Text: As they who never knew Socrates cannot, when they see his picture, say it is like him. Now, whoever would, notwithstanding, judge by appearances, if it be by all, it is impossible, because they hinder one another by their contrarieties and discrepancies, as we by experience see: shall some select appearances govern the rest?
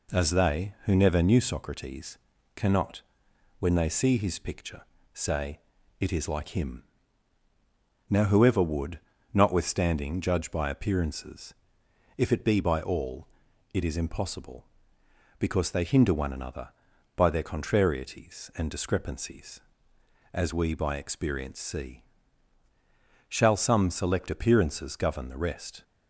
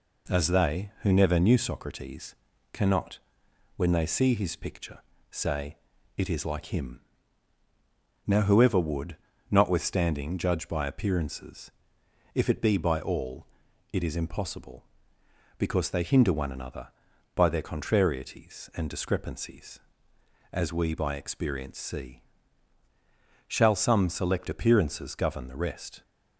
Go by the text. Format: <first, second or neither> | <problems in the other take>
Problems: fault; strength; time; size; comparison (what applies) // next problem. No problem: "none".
neither | pauses between "Socrates" and "cannot"; the same in both // pauses between "say" and "it"; the same in both